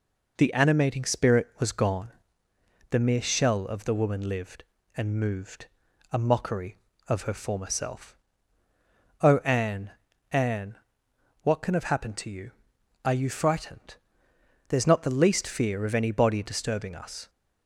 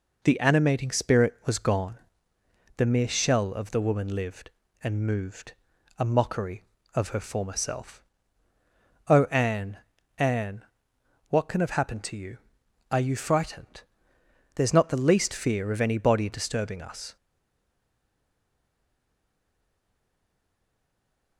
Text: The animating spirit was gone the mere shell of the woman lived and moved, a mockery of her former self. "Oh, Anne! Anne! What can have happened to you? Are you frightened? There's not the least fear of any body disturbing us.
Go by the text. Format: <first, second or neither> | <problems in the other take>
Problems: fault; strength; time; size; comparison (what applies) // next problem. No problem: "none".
first | pauses between "gone" and "the"; noticeable; at 1.9 s; 0.80 s long; noticeable in the first // stays silent after the last word; strong; from 17.1 s on; 4.2 s long